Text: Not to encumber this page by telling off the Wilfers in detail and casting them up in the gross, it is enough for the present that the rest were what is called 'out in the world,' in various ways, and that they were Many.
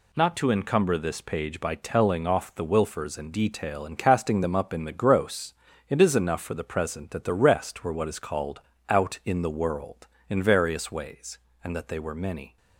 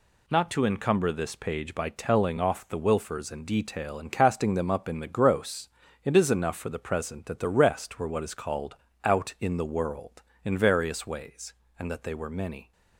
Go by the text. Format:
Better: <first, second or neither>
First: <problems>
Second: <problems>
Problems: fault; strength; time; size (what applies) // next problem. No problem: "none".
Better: neither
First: pauses between "called" and "out"; slight; at 8.6 s; 0.28 s long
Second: pauses between "called" and "out"; slight; at 8.7 s; 0.28 s long